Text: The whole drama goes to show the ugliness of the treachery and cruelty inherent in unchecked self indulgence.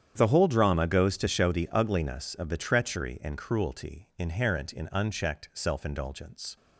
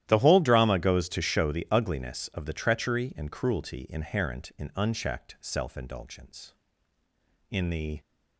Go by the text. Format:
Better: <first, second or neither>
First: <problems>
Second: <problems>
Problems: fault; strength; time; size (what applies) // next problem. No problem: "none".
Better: first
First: starts louder than the rest; strong; until 1.1 s; 9 dB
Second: starts louder than the rest; strong; until 1.0 s; 12.5 dB // goes on to say "In the"; from 7.4 s on; 0.50 s long